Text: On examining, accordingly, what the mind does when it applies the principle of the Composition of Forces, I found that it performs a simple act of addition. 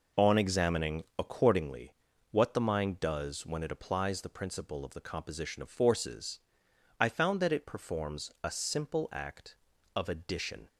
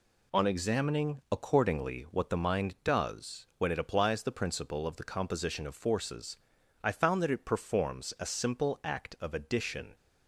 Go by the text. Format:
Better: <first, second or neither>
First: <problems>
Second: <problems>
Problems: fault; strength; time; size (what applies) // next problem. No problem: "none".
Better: second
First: starts louder than the rest; noticeable; until 1.7 s; 5 dB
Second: none